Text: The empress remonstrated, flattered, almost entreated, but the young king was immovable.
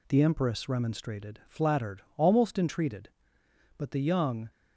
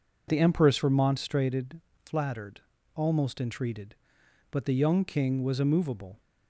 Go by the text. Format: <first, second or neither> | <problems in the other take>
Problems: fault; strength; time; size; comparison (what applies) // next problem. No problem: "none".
second | stops before "king was immovable"; at 4.5 s